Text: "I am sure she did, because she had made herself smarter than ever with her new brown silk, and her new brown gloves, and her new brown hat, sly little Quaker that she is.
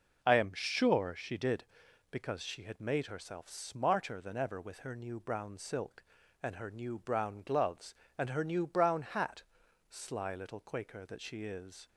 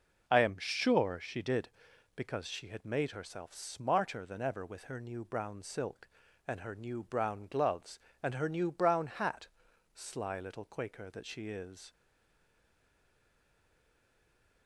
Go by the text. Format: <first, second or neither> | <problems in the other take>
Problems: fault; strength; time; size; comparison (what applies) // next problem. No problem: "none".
first | stays silent after the last word; strong; from 11.9 s on; 2.7 s long